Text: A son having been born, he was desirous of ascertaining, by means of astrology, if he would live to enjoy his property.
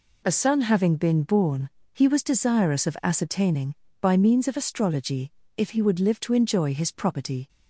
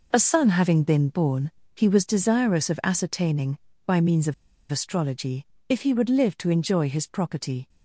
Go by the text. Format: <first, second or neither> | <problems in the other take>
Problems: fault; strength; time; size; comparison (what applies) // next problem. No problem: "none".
first | pauses between "of" and "astrology"; at 4.3 s; 0.36 s long